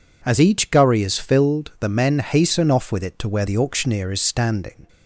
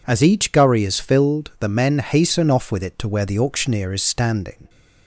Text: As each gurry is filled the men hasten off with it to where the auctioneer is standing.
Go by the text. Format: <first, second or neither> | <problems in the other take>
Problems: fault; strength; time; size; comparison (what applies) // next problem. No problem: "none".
neither | none